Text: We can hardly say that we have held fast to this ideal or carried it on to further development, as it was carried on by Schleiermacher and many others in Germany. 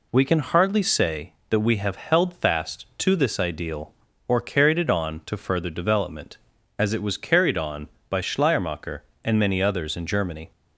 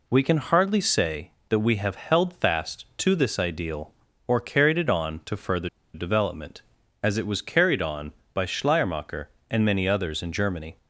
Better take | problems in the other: first | pauses between "further" and "development"; slight; at 5.6 s; 0.25 s long

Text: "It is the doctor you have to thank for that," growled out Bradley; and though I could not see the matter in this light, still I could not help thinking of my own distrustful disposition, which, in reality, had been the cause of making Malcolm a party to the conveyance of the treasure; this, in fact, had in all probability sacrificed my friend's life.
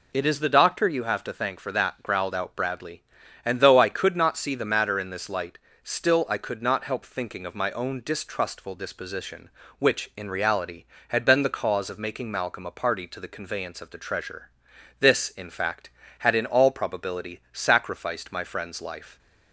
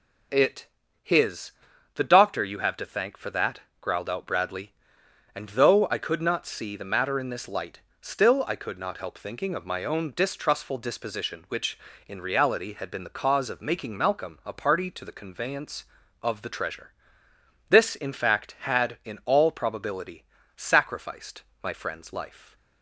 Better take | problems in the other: first | says "his" for "is"; at 1.0 s // pauses between "probability" and "sacrificed"; slight; at 20.2 s; 0.30 s long // pauses between "sacrificed" and "my"; slight; at 21.4 s; 0.22 s long

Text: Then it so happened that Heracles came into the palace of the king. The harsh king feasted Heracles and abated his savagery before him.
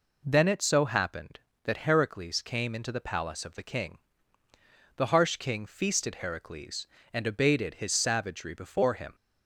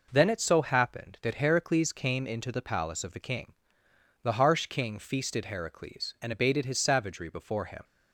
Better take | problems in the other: neither | none

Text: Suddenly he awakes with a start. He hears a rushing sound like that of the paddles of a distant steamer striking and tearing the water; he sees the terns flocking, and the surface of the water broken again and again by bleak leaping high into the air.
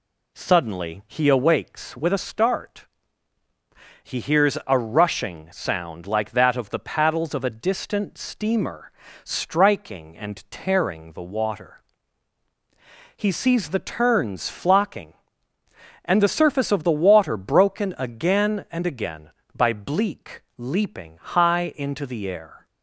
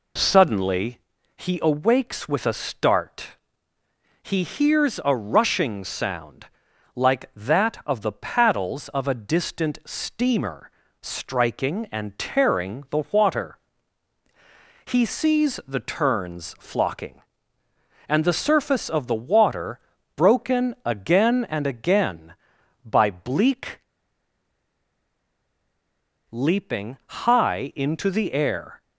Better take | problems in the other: first | pauses between "Suddenly" and "he"; at 0.9 s; 0.40 s long // pauses between "sound" and "like"; noticeable; at 6.4 s; 0.48 s long // pauses between "steamer" and "striking"; slight; at 10.7 s; 0.32 s long; slight in the first // pauses between "water" and "broken"; slight; at 19.7 s; 0.36 s long // pauses between "bleak" and "leaping"; strong; at 23.8 s; 2.4 s long

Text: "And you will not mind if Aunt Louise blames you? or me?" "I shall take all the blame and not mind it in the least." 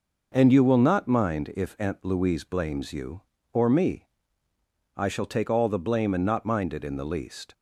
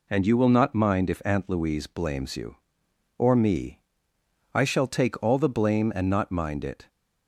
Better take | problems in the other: first | stops before "in the least"; at 6.8 s

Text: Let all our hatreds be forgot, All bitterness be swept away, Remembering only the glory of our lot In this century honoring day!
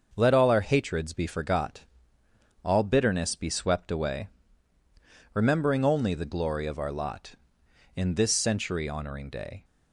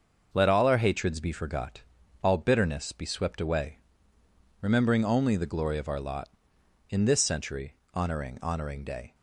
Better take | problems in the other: first | starts louder than the rest; until 1.3 s; 6.5 dB; also in the first // pauses between "century" and "honoring"; slight; at 7.7 s; 0.18 s long // says "honoring" twice; at 8.4 s

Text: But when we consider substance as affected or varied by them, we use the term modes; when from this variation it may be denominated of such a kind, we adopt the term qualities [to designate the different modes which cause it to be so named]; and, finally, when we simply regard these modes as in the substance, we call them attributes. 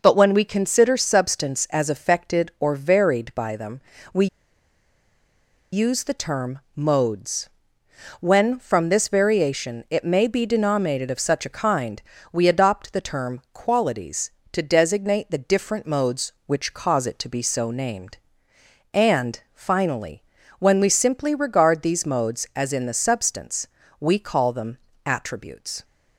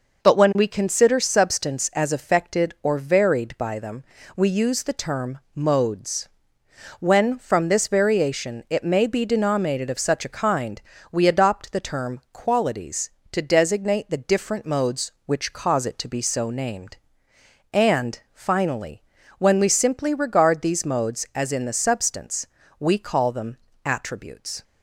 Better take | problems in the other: second | pauses between "we" and "use"; strong; at 4.2 s; 1.4 s long // pauses between "them" and "attributes"; slight; at 24.7 s; 0.28 s long; slight in the second

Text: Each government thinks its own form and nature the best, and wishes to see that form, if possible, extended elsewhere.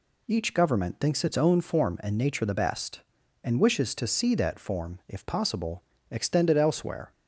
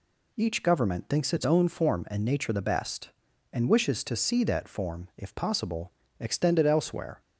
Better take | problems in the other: neither | none

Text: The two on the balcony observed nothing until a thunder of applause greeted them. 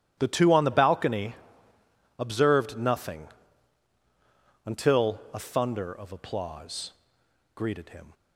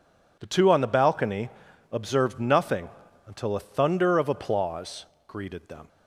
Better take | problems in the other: second | starts louder than the rest; strong; until 1.2 s; 11.5 dB // pauses between "balcony" and "observed"; noticeable; at 1.3 s; 0.82 s long; also in the second // pauses between "nothing" and "until"; strong; at 3.2 s; 1.3 s long; slight in the second // pauses between "applause" and "greeted"; noticeable; at 6.9 s; 0.62 s long; slight in the second // says "him" for "them"; at 7.8 s

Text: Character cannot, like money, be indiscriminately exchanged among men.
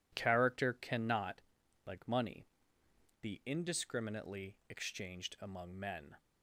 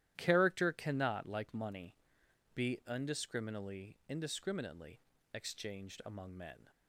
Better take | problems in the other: first | starts louder than the rest; strong; until 1.1 s; 13 dB // says "indiscriminately" twice; at 4.0 s

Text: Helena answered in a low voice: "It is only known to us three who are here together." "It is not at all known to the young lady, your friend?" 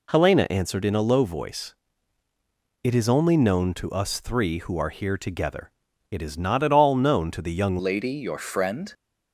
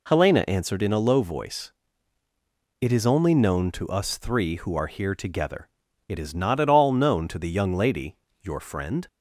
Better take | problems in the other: second | changes voice at "lady"; from 7.7 s on; 1.2 s long

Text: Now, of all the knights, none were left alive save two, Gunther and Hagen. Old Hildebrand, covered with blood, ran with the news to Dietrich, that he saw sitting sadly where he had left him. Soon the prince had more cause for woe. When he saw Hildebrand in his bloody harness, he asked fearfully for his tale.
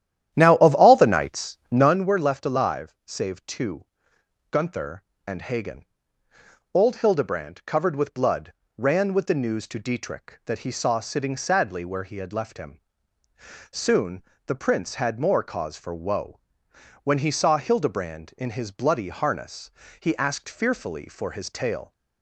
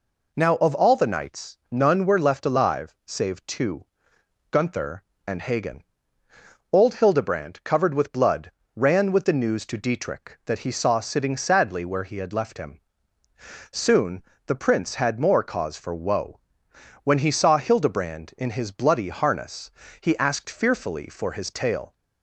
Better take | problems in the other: second | starts louder than the rest; strong; until 1.9 s; 11 dB // pauses between "Soon" and "the"; slight; at 14.2 s; 0.24 s long; slight in the second

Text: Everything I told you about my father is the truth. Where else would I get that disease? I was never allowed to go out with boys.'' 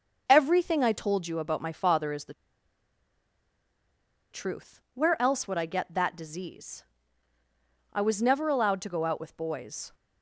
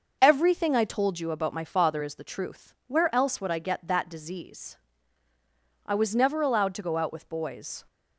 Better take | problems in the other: second | starts louder than the rest; noticeable; until 1.2 s; 6 dB; noticeable in the second // pauses between "the" and "truth"; strong; at 2.3 s; 1.9 s long

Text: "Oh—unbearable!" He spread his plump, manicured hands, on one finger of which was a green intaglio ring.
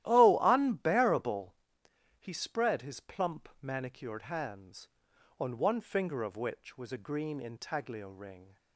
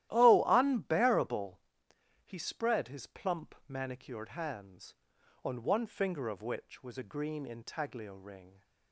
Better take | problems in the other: neither | starts louder than the rest; strong; the same in both

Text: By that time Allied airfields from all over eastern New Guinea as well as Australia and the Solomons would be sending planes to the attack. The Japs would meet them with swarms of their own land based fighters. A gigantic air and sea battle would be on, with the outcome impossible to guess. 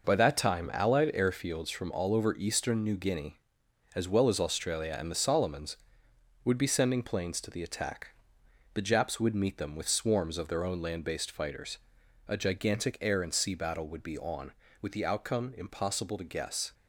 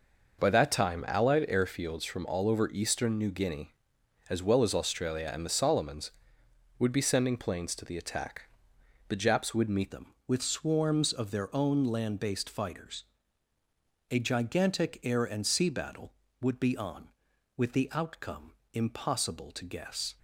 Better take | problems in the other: first | changes voice at "them"; from 9.9 s on; 10.2 s long // pauses between "outcome" and "impossible"; slight; at 18.5 s; 0.22 s long

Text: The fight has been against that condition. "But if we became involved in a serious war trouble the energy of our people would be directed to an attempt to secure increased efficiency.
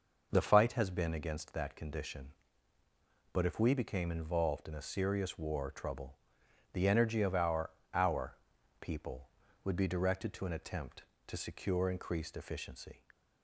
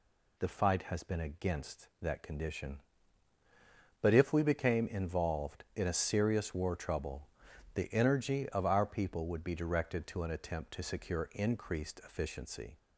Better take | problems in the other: second | pauses between "trouble" and "the"; noticeable; at 6.1 s; 0.54 s long; also in the second // says "our" twice; at 7.9 s

